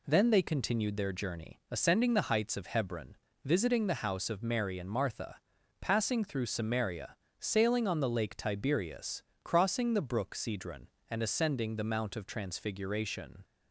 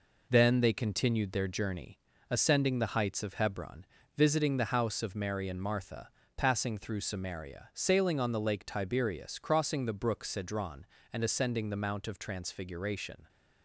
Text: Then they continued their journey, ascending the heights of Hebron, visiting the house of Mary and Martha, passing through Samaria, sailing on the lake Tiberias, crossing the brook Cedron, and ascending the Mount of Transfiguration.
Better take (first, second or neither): first